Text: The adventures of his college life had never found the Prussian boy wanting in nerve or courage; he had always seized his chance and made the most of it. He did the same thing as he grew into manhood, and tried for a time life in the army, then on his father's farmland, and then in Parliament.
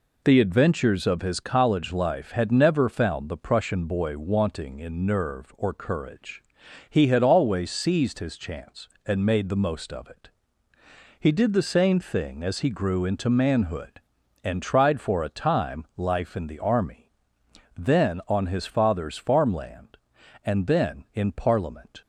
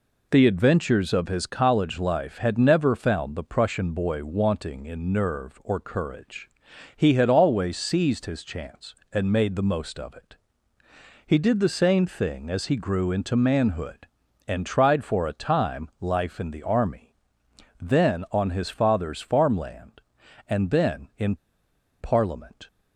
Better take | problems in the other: first | pauses between "in" and "Parliament"; noticeable; at 21.3 s; 0.63 s long

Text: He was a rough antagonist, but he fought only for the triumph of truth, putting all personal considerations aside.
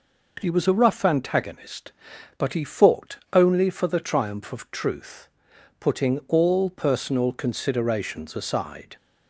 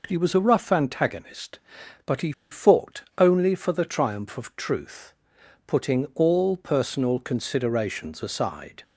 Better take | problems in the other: first | pauses between "he" and "fought"; slight; at 2.3 s; 0.19 s long // pauses between "fought" and "only"; slight; at 3.0 s; 0.16 s long; slight in the first

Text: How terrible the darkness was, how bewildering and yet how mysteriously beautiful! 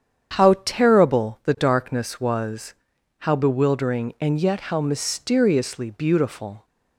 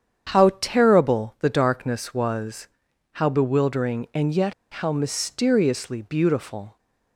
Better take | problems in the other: first | starts louder than the rest; strong; until 1.4 s; 8.5 dB; strong in the first // pauses between "yet" and "how"; slight; at 4.5 s; 0.19 s long

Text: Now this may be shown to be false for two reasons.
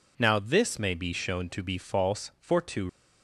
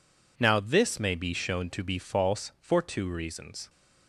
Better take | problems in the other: second | stops before "reasons"; at 2.8 s

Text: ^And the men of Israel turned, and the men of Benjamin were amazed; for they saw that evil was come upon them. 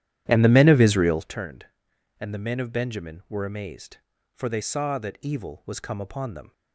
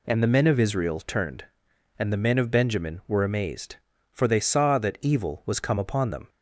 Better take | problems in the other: second | starts louder than the rest; strong; until 1.3 s; 11.5 dB

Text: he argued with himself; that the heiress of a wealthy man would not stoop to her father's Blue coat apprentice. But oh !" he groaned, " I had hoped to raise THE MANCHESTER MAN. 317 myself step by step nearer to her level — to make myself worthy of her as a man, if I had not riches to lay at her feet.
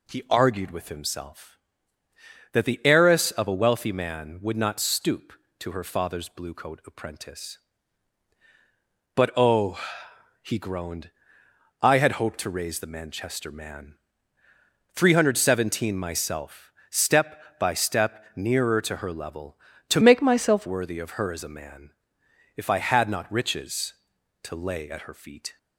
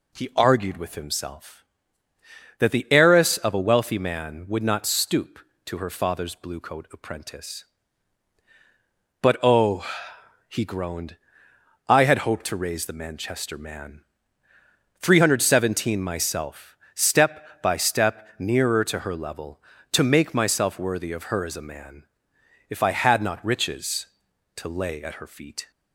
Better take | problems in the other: second | pauses between "myself" and "step"; slight; at 16.7 s; 0.18 s long; slight in the second // changes voice from "make" to "myself"; from 20.0 to 20.6 s; 0.6 s long

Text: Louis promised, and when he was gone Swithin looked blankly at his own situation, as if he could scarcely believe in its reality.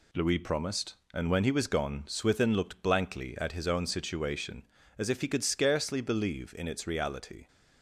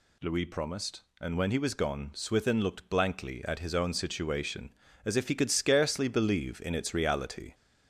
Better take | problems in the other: first | gets louder; slight; throughout; 3 dB

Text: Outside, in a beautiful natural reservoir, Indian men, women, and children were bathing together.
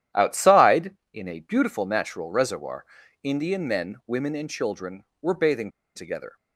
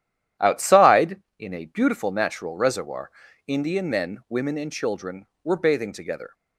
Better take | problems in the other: second | starts louder than the rest; strong; until 1.3 s; 11.5 dB; strong in the second // pauses between "bathing" and "together"; slight; at 5.6 s; 0.26 s long

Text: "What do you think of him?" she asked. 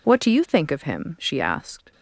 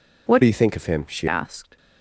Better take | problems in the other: first | changes voice from "do" to "she"; from 0.4 to 1.2 s; 0.8 s long

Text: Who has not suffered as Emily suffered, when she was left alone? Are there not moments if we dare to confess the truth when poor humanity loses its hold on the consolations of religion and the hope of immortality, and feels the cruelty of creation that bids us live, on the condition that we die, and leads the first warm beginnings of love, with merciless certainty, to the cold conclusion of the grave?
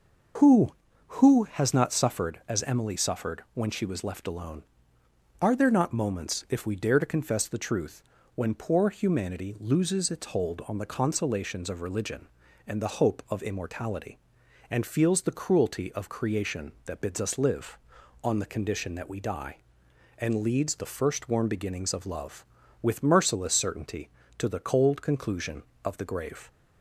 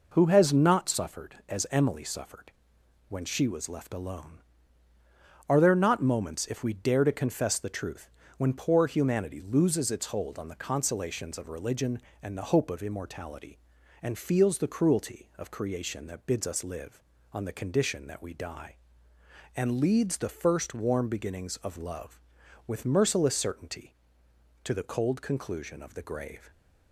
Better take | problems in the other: second | starts louder than the rest; noticeable; until 1.8 s; 6 dB // says "Who" twice; at 1.2 s // pauses between "truth" and "when"; slight; at 8.0 s; 0.32 s long; slight in the second

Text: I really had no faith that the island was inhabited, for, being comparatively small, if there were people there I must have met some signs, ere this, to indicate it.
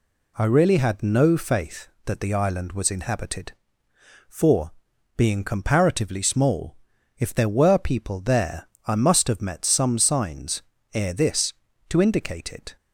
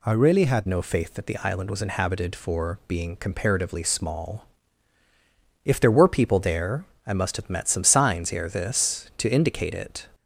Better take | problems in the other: first | changes voice at "no"; from 0.6 s on; 9.4 s long // pauses between "there" and "I"; slight; at 6.8 s; 0.24 s long; slight in the first

